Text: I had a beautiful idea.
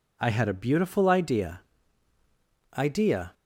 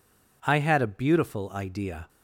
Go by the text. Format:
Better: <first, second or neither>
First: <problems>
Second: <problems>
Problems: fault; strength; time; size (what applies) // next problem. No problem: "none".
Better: second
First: says "idea" twice; at 2.7 s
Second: none